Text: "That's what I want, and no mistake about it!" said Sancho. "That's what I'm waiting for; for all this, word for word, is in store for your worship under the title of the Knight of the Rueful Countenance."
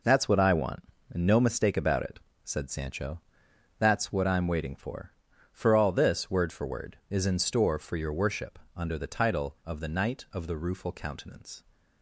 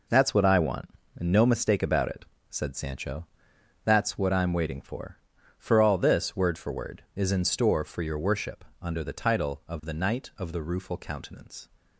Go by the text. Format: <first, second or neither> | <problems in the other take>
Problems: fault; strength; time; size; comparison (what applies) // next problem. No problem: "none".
neither | pauses between "worship" and "under"; slight; the same in both